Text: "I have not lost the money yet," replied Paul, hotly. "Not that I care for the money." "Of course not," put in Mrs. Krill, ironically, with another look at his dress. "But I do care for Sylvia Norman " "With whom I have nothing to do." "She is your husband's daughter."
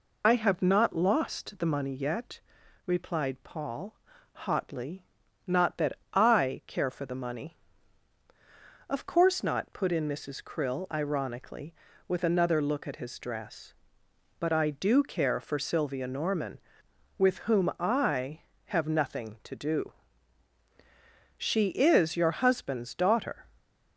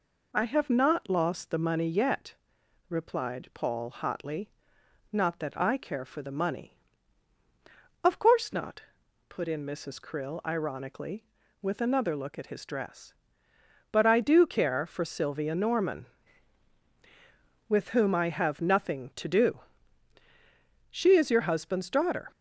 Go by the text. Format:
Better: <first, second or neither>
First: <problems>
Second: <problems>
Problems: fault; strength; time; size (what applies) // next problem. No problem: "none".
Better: second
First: loses the start of "I"; at 0.2 s; 45 ms // pauses between "that" and "I"; slight; at 5.9 s; 0.18 s long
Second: none